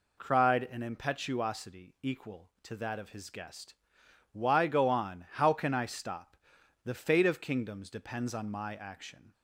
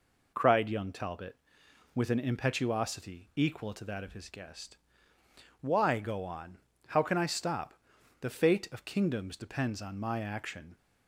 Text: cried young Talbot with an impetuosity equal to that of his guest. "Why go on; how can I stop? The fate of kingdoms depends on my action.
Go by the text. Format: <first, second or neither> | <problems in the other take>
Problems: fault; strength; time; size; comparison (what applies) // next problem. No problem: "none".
second | skips "young Talbot with"; at 0.6 s